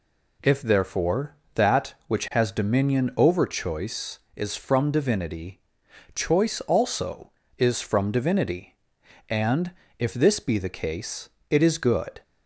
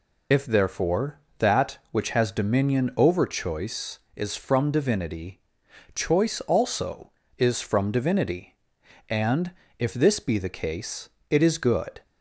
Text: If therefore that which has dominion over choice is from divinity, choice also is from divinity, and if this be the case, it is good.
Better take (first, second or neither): first